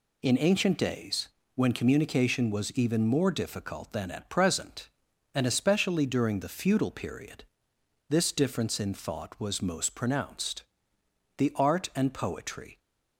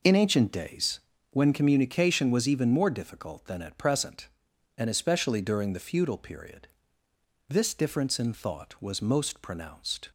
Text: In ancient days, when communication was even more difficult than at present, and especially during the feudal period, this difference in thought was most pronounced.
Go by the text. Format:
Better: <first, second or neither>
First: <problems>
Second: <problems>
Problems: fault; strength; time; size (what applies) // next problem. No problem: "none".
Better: second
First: goes on to say "The art and poetry"; from 11.3 s on; 1.4 s long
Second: none